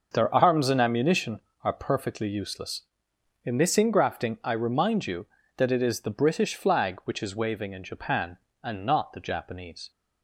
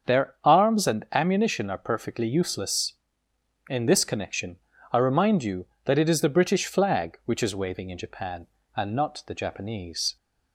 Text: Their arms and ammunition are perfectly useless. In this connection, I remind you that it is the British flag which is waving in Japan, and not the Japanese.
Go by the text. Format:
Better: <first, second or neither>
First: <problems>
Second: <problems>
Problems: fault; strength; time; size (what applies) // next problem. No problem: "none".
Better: second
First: starts louder than the rest; noticeable; until 1.1 s; 6 dB // says "ingrafting" for "connection"; at 3.7 s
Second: starts louder than the rest; until 1.2 s; 7 dB